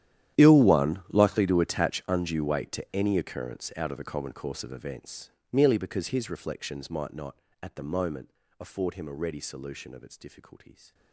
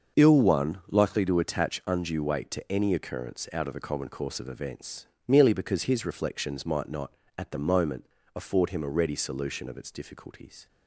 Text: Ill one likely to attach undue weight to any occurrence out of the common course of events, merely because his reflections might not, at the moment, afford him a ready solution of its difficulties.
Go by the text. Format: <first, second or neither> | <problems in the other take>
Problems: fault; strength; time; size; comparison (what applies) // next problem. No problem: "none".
second | gets quieter; strong; throughout; 20.5 dB // starts louder than the rest; strong; until 1.5 s; 11 dB; also in the second